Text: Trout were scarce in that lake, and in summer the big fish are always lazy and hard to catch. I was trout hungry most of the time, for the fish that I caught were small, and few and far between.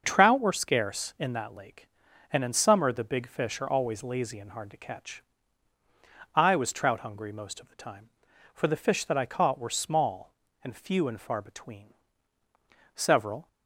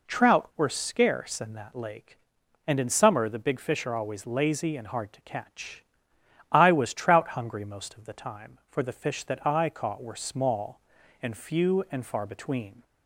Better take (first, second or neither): second